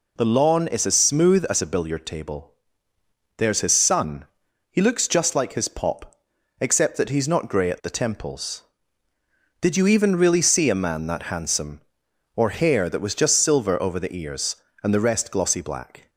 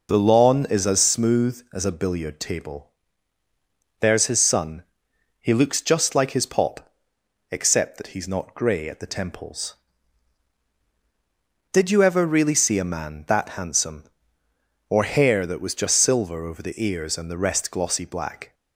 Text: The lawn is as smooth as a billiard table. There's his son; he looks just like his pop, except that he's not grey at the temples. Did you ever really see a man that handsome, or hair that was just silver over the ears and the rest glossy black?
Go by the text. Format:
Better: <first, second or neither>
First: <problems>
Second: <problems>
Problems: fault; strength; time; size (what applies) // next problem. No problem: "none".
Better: second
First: says "even" for "ever"; at 9.8 s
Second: none